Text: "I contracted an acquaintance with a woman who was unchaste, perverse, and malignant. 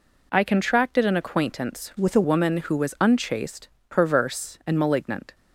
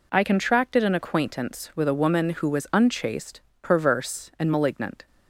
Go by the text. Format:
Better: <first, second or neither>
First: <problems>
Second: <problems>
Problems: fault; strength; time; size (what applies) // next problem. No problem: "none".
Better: second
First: changes voice from "with" to "a"; from 1.9 to 2.2 s; 0.3 s long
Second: none